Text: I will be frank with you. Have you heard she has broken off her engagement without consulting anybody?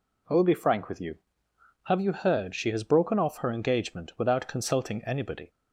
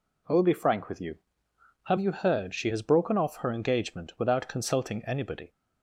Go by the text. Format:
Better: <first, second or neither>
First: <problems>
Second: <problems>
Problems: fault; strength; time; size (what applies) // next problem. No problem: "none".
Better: neither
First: none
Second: none